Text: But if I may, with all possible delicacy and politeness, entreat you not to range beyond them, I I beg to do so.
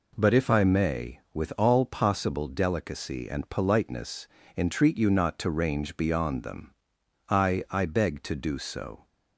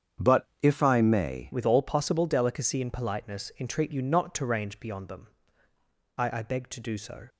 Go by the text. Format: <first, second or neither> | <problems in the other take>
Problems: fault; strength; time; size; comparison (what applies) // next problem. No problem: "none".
first | starts louder than the rest; strong; until 1.3 s; 8 dB // changes voice at "with"; from 1.5 s on; 5.7 s long